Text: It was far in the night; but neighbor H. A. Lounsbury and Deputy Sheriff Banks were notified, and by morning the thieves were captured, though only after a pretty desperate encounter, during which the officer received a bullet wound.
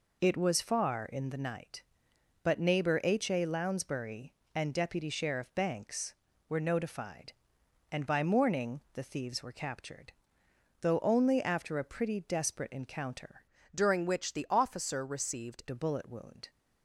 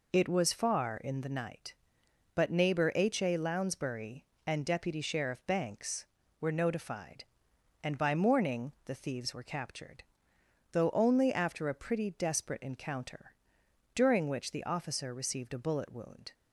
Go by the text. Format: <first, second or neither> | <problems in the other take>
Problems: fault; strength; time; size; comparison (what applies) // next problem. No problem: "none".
second | changes voice from "during" to "received"; from 13.7 to 15.6 s; 1.9 s long